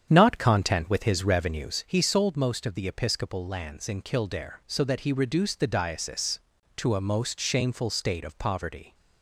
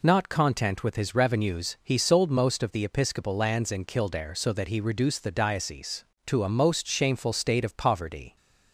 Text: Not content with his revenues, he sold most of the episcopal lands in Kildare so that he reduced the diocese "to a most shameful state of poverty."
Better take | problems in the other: second | starts louder than the rest; strong; until 1.9 s; 8.5 dB

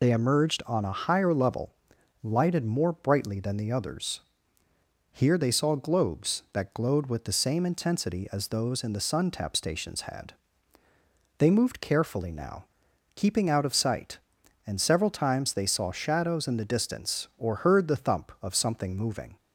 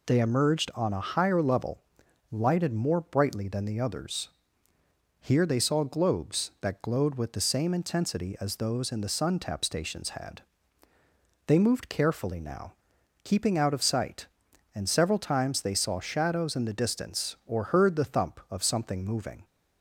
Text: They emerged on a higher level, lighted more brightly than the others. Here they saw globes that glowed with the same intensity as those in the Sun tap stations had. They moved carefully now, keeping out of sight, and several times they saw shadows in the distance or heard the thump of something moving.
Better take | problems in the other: second | loses the start of "They"; at 0.0 s; 35 ms

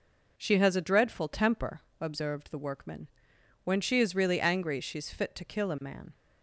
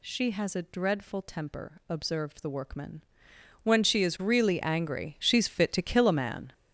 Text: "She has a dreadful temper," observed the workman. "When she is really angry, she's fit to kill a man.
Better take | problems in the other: first | gets louder; strong; throughout; 9.5 dB

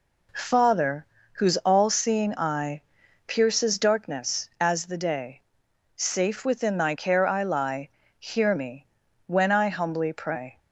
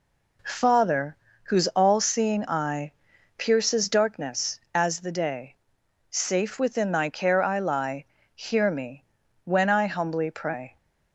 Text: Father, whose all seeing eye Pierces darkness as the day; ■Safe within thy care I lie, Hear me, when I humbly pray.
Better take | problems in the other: neither | pauses between "eye" and "Pierces"; noticeable; the same in both

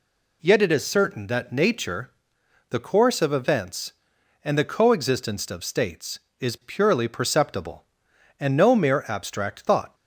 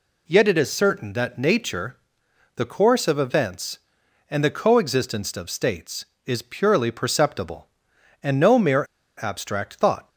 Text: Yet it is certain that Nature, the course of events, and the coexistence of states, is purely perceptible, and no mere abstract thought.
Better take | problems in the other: first | pauses between "mere" and "abstract"; slight; at 8.8 s; 0.33 s long

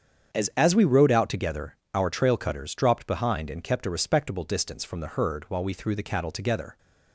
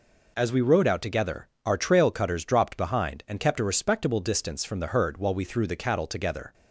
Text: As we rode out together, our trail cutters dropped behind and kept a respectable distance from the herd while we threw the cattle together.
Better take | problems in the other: second | starts louder than the rest; strong; until 1.4 s; 7.5 dB // says "As" twice; at 0.5 s

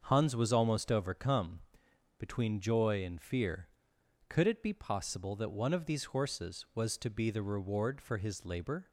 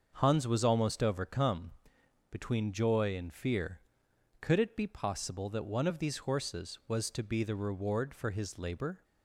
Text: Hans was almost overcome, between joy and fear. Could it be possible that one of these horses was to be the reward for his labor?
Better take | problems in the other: neither | starts louder than the rest; the same in both

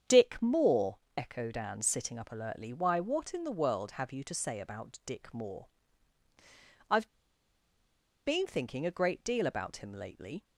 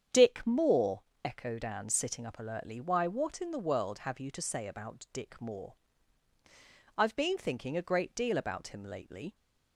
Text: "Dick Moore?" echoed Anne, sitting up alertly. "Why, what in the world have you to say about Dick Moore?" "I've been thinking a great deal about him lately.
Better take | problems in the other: second | starts louder than the rest; strong; until 1.2 s; 8 dB; strong in the second // pauses between "I've" and "been"; at 7.0 s; 1.1 s long

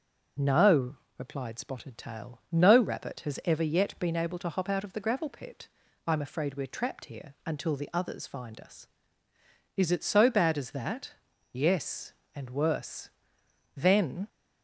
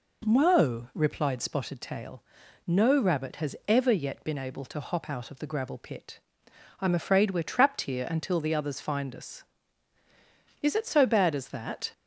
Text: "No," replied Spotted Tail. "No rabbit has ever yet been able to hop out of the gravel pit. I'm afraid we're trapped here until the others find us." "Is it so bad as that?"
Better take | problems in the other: second | goes on to say "Yes and worse Then"; strong; from 11.5 s on; 2.7 s long

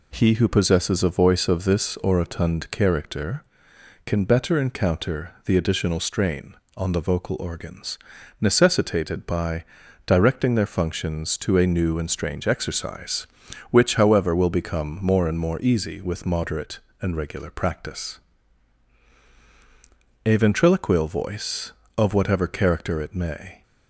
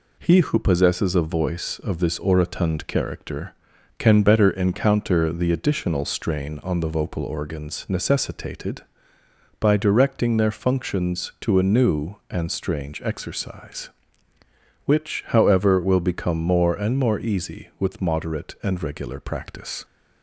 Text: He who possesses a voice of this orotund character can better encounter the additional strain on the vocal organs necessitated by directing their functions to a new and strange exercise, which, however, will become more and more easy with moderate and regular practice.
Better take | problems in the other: second | pauses between "organs" and "necessitated"; at 7.9 s; 0.42 s long // pauses between "by" and "directing"; at 9.6 s; 0.40 s long // goes on to say "A ventriloquial voice of whatever character it may"; strong; from 20.2 s on; 3.3 s long

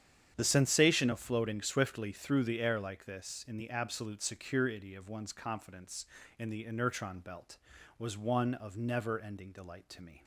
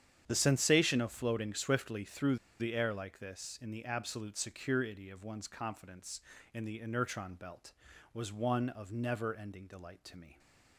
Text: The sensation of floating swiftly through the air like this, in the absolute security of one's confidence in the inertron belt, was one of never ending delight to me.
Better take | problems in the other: first | starts louder than the rest; strong; until 1.2 s; 9 dB; strong in the first // pauses between "through" and "the"; slight; at 2.3 s; 0.22 s long

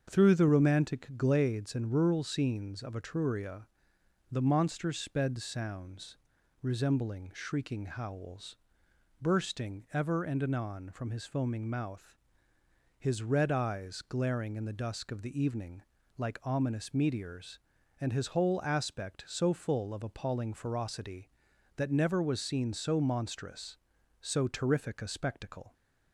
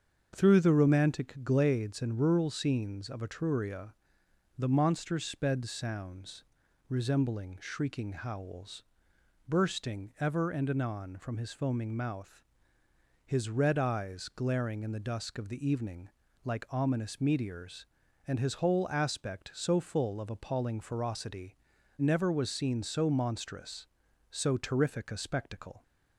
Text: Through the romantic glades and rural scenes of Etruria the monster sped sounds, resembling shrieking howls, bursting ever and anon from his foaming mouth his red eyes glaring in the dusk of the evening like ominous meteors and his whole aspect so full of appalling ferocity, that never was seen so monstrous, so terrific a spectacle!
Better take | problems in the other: first | starts louder than the rest; strong; until 1.3 s; 7 dB; strong in the first // pauses between "Etruria" and "the"; noticeable; at 3.9 s; 0.64 s long; noticeable in the first // pauses between "mouth" and "his"; noticeable; at 12.4 s; 0.82 s long; noticeable in the first // pauses between "evening" and "like"; slight; at 16.0 s; 0.36 s long; slight in the first // skips "that"; at 21.7 s

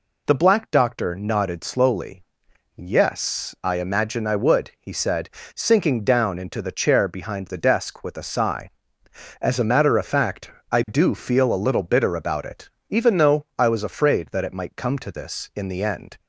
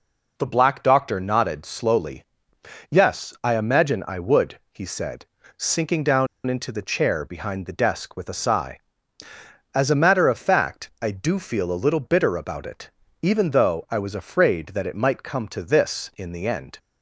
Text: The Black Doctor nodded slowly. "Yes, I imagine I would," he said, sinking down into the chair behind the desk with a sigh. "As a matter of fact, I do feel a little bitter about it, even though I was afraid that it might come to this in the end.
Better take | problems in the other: first | pauses between "down" and "into"; slight; at 6.2 s; 0.20 s long

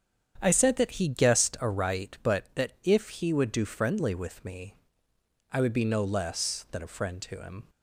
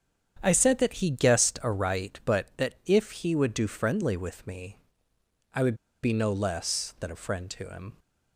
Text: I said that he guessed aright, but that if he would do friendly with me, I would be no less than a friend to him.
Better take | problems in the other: first | starts louder than the rest; strong; until 1.4 s; 8 dB; strong in the first // pauses between "would" and "be"; slight; at 5.7 s; 0.27 s long

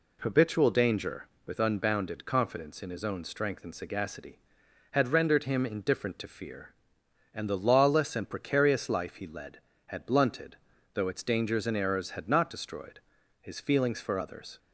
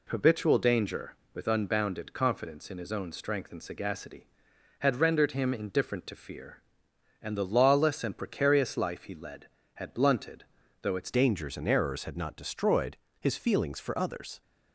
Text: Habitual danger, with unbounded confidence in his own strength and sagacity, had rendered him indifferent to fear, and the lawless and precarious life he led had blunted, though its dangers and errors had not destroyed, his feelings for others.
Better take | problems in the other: first | changes voice at "dangers"; from 11.1 s on; 3.3 s long

